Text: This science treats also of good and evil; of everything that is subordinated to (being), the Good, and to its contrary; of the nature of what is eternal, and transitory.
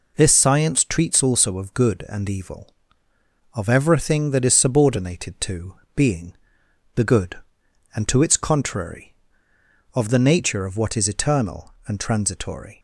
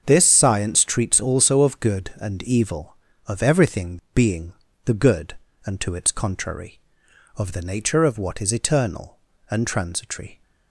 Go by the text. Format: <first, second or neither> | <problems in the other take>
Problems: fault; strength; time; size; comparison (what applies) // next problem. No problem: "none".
first | starts louder than the rest; noticeable; until 1.0 s; 6 dB // skips "that is subordinated to"; at 4.0 s